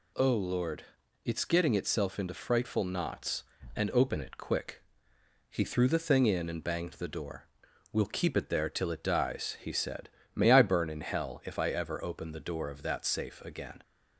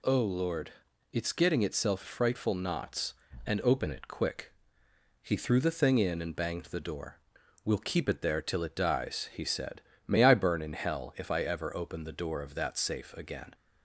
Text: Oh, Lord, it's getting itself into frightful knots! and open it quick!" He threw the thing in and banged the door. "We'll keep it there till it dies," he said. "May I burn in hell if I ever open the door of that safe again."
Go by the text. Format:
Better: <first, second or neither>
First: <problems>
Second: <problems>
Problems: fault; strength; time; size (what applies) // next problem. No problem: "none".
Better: first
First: none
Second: skips "into"; at 2.0 s